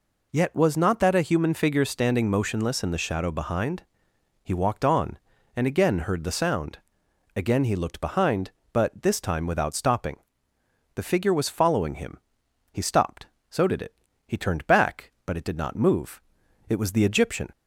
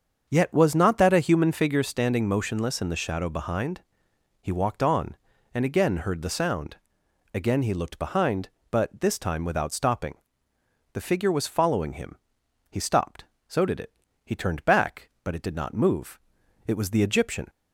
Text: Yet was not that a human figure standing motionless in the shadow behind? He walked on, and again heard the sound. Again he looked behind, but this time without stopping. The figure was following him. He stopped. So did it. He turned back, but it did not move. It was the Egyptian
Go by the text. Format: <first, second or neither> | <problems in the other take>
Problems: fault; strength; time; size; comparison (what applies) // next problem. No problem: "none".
first | starts louder than the rest; until 1.7 s; 6.5 dB